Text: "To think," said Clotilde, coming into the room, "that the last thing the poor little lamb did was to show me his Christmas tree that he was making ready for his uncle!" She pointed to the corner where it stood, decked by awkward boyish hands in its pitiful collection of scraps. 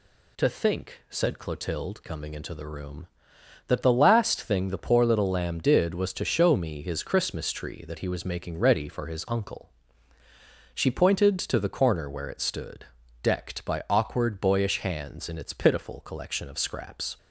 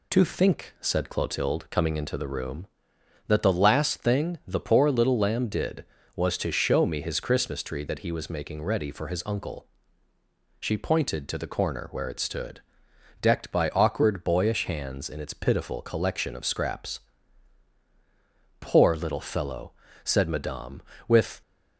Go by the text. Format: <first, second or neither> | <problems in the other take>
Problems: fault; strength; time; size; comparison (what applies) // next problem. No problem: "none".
first | goes on to say "Poor little fellow said madame with"; strong; from 18.6 s on; 2.8 s long